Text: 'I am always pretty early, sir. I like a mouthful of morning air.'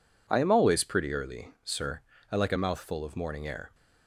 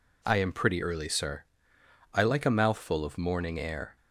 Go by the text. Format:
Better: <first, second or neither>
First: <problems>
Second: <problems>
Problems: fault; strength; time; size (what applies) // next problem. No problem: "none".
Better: first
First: none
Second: skips "always"; at 0.5 s